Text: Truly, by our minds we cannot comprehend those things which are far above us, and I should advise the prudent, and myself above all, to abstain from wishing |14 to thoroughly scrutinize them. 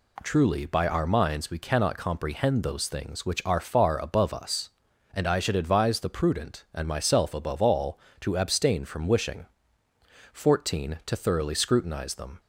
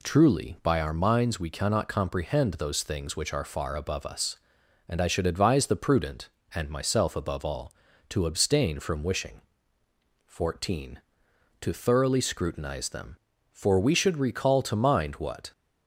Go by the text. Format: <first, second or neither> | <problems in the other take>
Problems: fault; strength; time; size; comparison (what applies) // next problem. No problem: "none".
first | goes on to say "For we should recall to mind what"; strong; from 13.5 s on; 2.0 s long